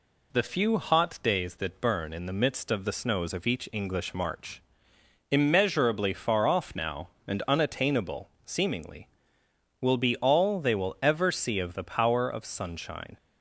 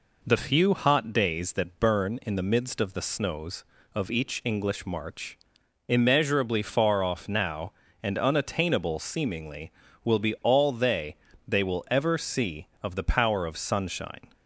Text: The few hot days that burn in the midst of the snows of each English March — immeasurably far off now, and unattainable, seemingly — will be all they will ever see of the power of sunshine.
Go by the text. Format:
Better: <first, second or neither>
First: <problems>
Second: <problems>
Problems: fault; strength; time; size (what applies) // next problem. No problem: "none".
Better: first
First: none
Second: says "they" twice; at 11.4 s